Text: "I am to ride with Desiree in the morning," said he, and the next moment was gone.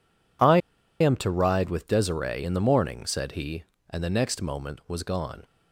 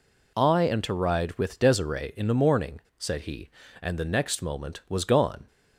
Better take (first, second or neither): second